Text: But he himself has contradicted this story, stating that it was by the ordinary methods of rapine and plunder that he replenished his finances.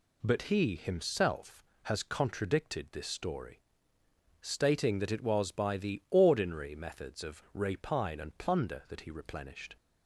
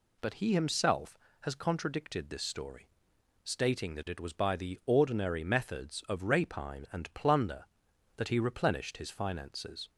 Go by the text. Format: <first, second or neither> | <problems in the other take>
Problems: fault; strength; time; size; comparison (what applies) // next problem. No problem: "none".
second | stops before "his finances"; at 9.7 s